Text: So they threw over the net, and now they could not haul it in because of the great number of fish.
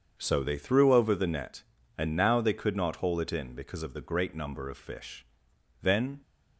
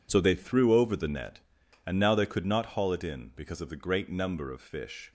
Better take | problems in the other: second | starts louder than the rest; until 1.1 s; 7 dB // goes on to say "Then"; slight; from 5.7 s on; 0.40 s long

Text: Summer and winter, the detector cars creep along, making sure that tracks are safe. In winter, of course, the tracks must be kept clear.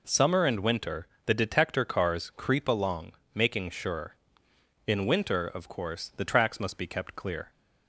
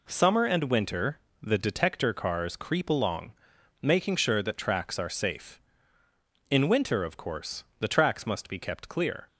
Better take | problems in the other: second | skips "that tracks are safe"; at 4.4 s

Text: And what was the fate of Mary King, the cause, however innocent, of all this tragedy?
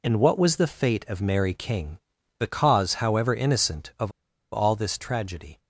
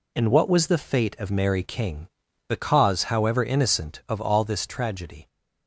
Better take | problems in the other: second | pauses between "of" and "all"; at 4.1 s; 0.41 s long

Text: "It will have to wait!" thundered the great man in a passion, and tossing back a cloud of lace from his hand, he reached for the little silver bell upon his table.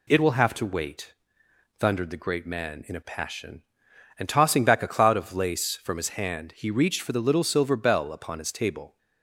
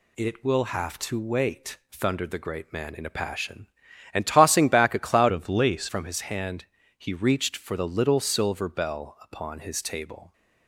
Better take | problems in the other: first | changes voice from "of" to "lace"; from 5.2 to 5.8 s; 0.6 s long

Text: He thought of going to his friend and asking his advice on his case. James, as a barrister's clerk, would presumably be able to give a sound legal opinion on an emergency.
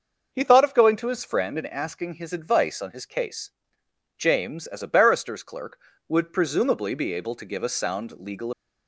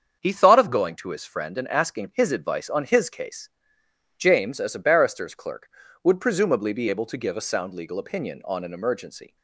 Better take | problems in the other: second | starts louder than the rest; until 1.3 s; 6 dB; strong in the second // stops before "opinion on an emergency"; at 8.5 s

